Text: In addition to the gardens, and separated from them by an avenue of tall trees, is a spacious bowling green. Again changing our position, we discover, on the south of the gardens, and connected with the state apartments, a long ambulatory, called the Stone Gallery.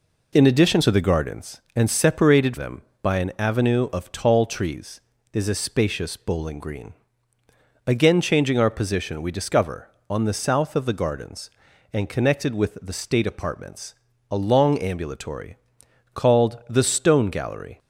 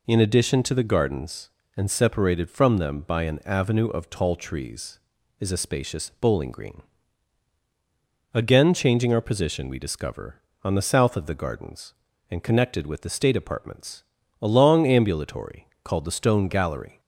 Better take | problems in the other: second | skips "from"; at 2.5 s

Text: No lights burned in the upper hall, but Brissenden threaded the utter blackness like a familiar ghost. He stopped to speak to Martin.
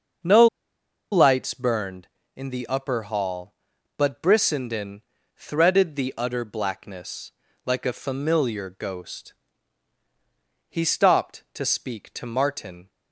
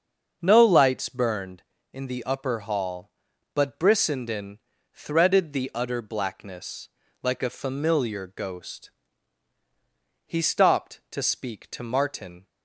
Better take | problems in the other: second | starts louder than the rest; until 1.9 s; 6.5 dB; also in the second // pauses between "No" and "lights"; noticeable; at 0.4 s; 0.66 s long // pauses between "Brissenden" and "threaded"; slight; at 5.0 s; 0.36 s long; slight in the second // pauses between "blackness" and "like"; slight; at 7.3 s; 0.34 s long; slight in the second

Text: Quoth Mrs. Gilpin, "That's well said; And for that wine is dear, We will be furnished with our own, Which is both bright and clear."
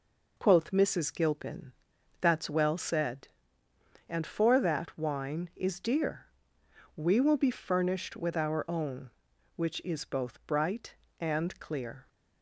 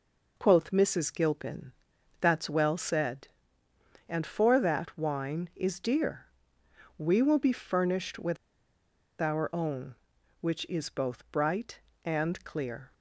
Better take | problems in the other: first | pauses between "with" and "our"; noticeable; at 8.3 s; 0.84 s long

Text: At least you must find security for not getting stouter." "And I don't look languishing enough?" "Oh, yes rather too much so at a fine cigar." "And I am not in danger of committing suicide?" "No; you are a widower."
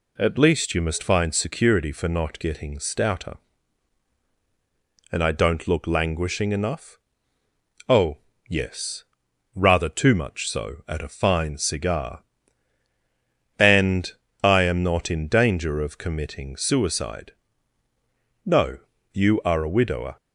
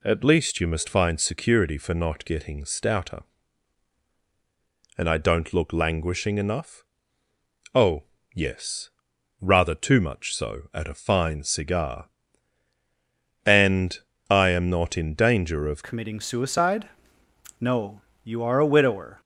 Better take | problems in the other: first | pauses between "yes" and "rather"; noticeable; at 8.8 s; 0.54 s long; noticeable in the first // pauses between "And" and "I"; slight; at 13.9 s; 0.32 s long; slight in the first // changes voice at "committing"; from 15.8 s on; 3.4 s long

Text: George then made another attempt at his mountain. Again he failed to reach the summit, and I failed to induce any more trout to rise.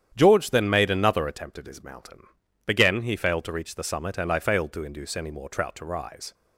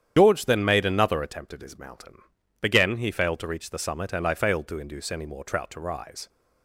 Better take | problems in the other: first | loses the start of "George"; at 0.1 s; 95 ms // starts louder than the rest; strong; until 1.1 s; 9 dB; strong in the first

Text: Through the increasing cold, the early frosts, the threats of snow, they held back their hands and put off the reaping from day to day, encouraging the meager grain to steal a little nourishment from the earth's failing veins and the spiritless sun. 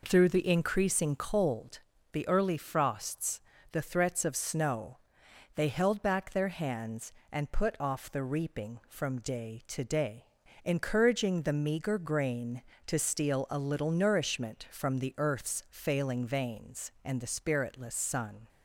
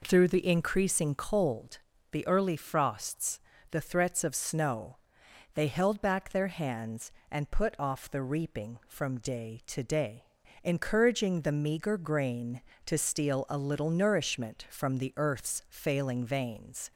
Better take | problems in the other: first | stops before "and the spiritless sun"; at 16.9 s

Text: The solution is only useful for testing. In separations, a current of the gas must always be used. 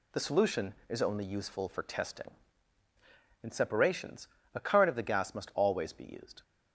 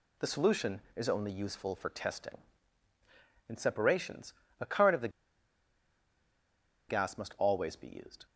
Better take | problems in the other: first | pauses between "the" and "gas"; strong; at 5.0 s; 1.7 s long

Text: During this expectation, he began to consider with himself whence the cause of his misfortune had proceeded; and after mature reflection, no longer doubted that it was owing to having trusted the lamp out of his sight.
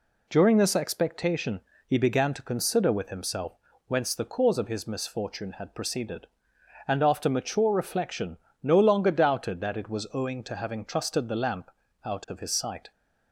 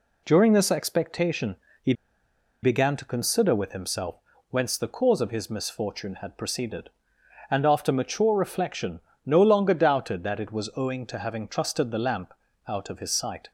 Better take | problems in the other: first | pauses between "he" and "began"; noticeable; at 1.9 s; 0.69 s long // pauses between "himself" and "whence"; slight; at 4.1 s; 0.34 s long; slight in the first // pauses between "lamp" and "out"; slight; at 12.3 s; 0.34 s long; slight in the first

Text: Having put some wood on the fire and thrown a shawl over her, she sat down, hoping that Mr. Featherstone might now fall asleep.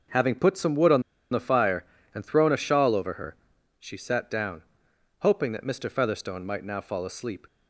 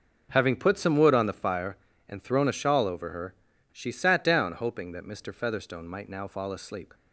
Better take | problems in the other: second | starts louder than the rest; noticeable; until 1.4 s; 6 dB // pauses between "on" and "the"; slight; at 1.0 s; 0.30 s long

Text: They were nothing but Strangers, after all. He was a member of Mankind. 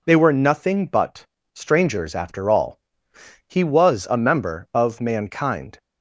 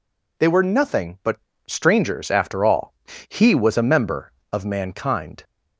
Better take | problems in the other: neither | pauses between "but" and "Strangers"; slight; the same in both

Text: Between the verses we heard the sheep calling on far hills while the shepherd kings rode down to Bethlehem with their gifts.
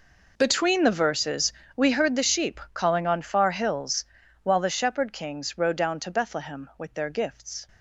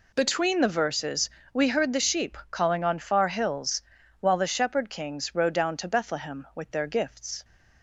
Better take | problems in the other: second | gets quieter; strong; throughout; 17.5 dB // pauses between "verses" and "we"; slight; at 1.5 s; 0.24 s long; slight in the second // pauses between "hills" and "while"; at 4.0 s; 0.40 s long; also in the second

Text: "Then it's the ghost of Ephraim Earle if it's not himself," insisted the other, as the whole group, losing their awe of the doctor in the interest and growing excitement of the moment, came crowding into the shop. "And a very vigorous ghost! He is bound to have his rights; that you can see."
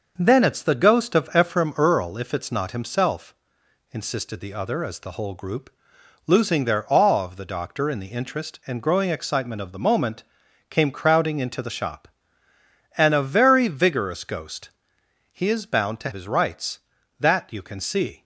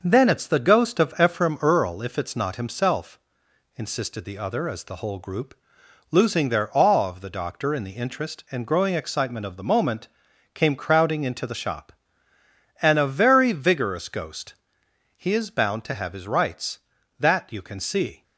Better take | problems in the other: second | starts louder than the rest; noticeable; until 1.1 s; 6 dB // skips "have"; at 16.1 s

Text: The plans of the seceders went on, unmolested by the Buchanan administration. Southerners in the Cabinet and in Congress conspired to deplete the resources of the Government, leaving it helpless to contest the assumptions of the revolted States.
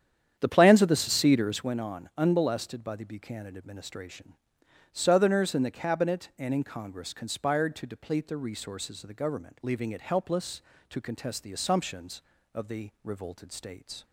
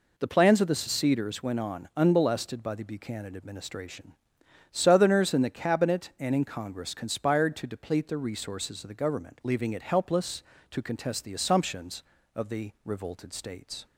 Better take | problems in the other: second | starts louder than the rest; strong; until 1.7 s; 9 dB

